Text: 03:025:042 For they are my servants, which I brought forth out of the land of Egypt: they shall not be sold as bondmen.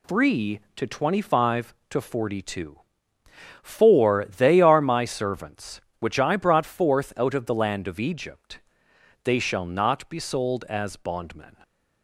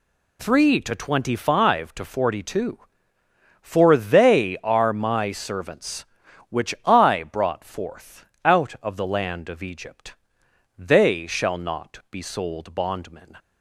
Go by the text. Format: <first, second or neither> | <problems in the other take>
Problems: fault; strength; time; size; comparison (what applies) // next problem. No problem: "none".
first | pauses between "forth" and "out"; slight; at 8.2 s; 0.18 s long // skips "as"; at 12.7 s